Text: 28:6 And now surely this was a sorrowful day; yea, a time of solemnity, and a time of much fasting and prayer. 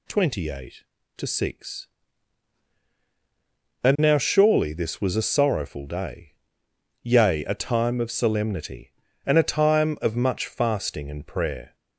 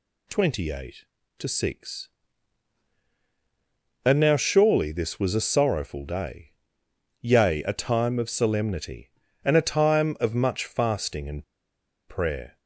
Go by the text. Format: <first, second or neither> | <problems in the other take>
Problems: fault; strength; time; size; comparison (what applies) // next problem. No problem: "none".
first | pauses between "and" and "prayer"; noticeable; at 11.4 s; 0.64 s long